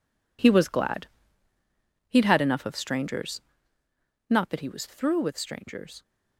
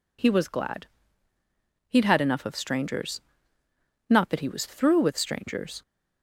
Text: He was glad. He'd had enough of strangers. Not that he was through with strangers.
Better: second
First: gets quieter; strong; throughout; 12 dB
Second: none

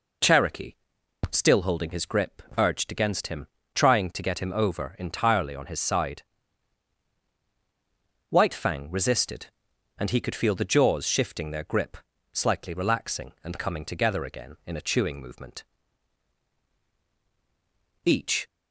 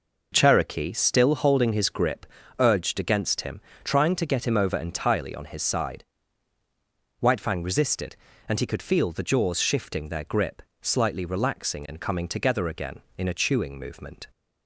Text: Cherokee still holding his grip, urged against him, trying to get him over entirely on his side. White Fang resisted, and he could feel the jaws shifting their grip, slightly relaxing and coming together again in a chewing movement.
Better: second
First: pauses between "Cherokee" and "still"; noticeable; at 0.7 s; 0.58 s long // goes on to say "Each"; slight; from 18.0 s on; 0.42 s long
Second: none

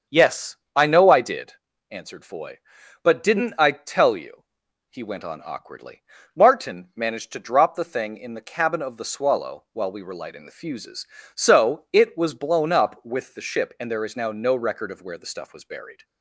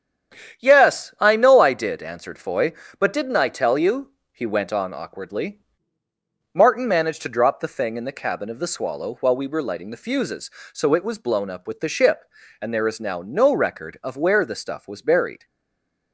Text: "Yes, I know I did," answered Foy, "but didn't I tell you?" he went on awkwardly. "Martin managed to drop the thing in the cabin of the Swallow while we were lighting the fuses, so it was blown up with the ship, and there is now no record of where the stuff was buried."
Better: first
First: starts louder than the rest; strong; until 1.2 s; 7 dB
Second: starts louder than the rest; strong; until 1.6 s; 9.5 dB // stays silent after the last word; slight; from 15.4 s on; 0.7 s long

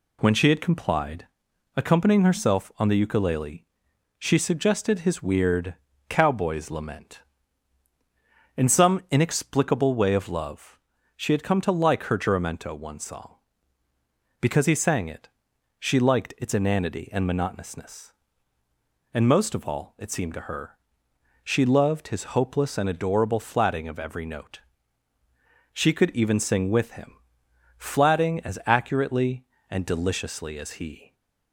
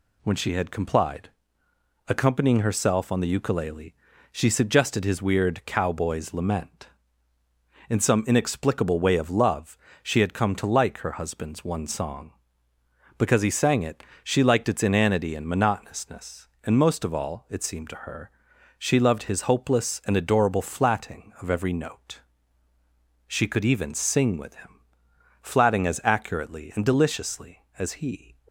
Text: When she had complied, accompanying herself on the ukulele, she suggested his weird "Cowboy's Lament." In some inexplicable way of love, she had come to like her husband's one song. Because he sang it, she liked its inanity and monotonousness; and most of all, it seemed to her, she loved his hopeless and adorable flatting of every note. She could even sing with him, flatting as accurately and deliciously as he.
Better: second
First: pauses between "weird" and "Cowboy's"; slight; at 5.7 s; 0.34 s long // says "juramento" for "husband's"; at 12.1 s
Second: none

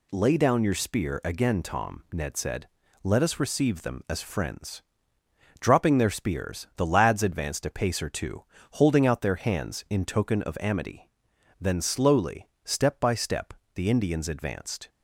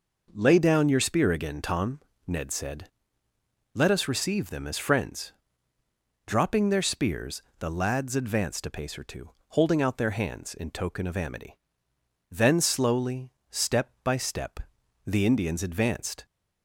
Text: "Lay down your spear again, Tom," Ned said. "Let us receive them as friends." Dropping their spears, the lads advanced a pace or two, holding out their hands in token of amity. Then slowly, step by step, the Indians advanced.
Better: neither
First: none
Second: none

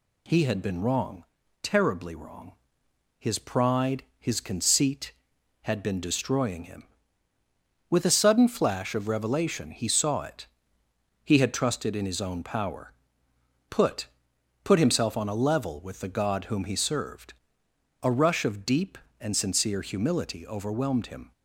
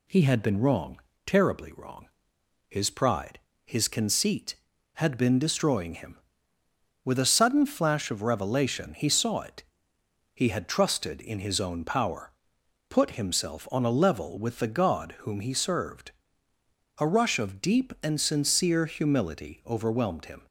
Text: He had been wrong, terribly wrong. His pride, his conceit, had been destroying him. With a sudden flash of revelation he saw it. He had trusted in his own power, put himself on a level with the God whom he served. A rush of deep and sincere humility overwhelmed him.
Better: second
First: says "put" twice; at 14.6 s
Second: none

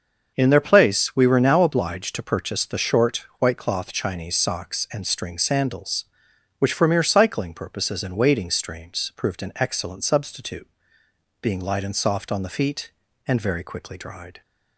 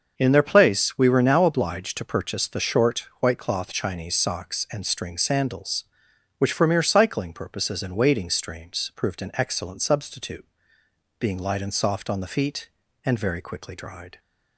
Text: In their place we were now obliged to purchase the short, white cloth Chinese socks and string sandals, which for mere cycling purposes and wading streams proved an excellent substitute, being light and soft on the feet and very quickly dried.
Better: neither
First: starts louder than the rest; until 1.3 s; 6.5 dB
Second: starts louder than the rest; until 1.1 s; 6.5 dB

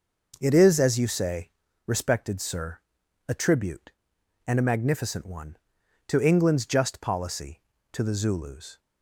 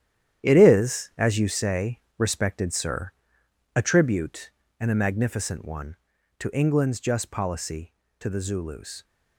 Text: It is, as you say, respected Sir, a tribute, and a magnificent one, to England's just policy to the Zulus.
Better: first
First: none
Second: gets quieter; strong; throughout; 10 dB

